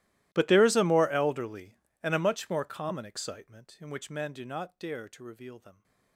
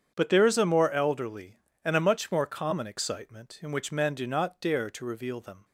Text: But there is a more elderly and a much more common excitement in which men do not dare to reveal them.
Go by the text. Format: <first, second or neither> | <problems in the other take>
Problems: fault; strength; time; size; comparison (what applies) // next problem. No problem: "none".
second | gets quieter; strong; throughout; 27 dB // starts louder than the rest; strong; until 1.3 s; 16 dB; strong in the second